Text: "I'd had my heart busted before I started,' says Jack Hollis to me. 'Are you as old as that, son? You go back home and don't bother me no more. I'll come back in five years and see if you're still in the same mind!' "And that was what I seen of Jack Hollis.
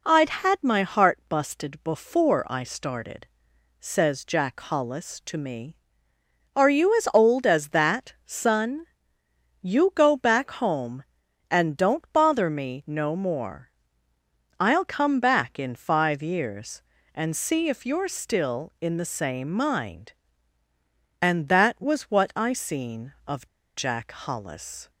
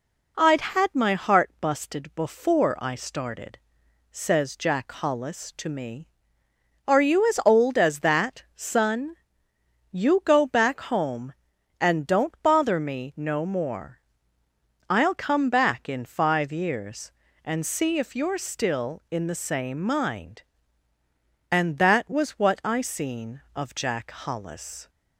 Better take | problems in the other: second | pauses between "of" and "Jack"; slight; at 23.4 s; 0.31 s long

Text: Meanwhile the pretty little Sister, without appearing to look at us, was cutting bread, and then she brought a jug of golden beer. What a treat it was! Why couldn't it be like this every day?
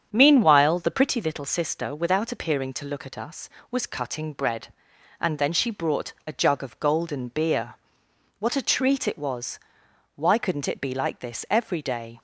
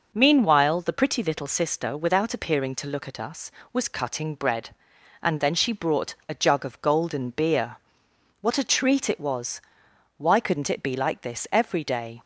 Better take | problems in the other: second | starts louder than the rest; strong; until 1.3 s; 8 dB

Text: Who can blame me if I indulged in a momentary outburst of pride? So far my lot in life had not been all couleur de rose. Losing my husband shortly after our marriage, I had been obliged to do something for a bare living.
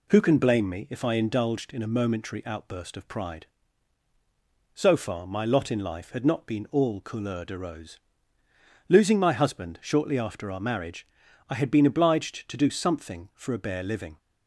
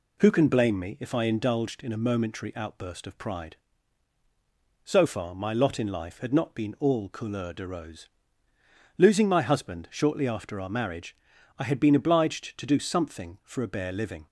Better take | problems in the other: neither | none

